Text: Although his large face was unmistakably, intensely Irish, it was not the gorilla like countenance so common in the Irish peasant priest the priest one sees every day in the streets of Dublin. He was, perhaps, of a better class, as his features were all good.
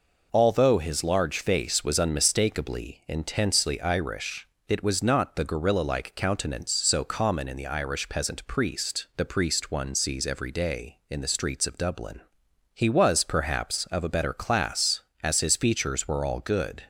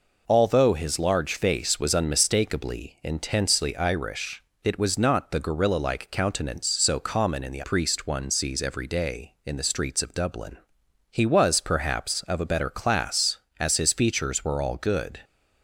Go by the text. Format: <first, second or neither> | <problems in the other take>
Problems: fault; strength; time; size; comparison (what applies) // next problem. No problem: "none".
first | skips "Irish peasant priest the"; at 7.6 s